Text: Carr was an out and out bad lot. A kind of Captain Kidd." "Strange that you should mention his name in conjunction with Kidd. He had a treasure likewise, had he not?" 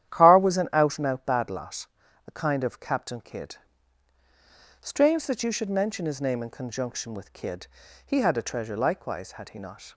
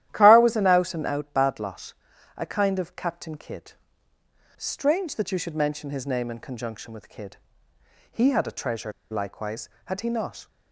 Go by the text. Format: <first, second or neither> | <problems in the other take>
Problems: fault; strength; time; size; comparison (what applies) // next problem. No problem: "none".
first | starts louder than the rest; strong; until 1.1 s; 12.5 dB; strong in the first // pauses between "treasure" and "likewise"; slight; at 8.9 s; 0.19 s long